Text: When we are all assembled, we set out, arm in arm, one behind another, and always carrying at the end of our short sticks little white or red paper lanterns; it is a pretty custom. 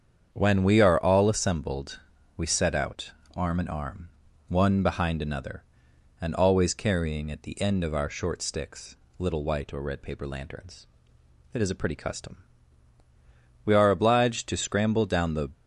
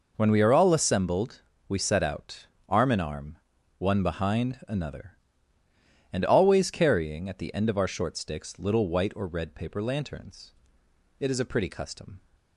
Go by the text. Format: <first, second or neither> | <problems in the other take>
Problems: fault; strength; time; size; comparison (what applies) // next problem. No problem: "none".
second | starts louder than the rest; strong; until 1.3 s; 7.5 dB // pauses between "sticks" and "little"; slight; at 8.9 s; 0.22 s long // goes on to say "We are obliged to scramble down the"; strong; from 13.6 s on; 1.8 s long